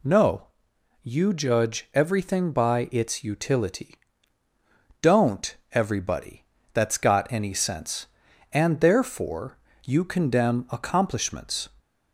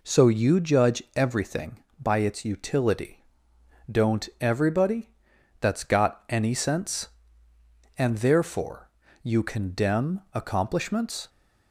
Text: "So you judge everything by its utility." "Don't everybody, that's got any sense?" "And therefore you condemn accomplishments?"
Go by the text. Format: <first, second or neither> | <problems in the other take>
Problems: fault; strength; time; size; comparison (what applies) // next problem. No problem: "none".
second | says "No" for "So"; at 0.0 s // pauses between "Don't" and "everybody"; slight; at 5.5 s; 0.16 s long // pauses between "therefore" and "you"; slight; at 9.5 s; 0.26 s long; slight in the second